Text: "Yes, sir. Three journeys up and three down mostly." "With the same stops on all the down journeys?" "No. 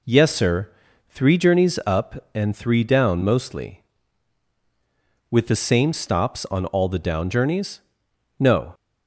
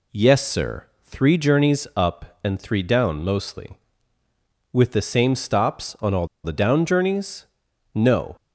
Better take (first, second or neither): first